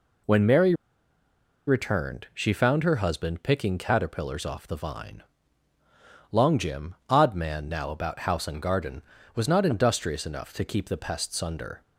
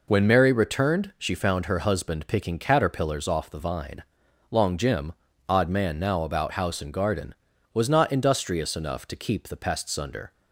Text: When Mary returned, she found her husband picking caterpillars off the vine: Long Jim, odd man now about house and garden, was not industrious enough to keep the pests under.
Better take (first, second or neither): second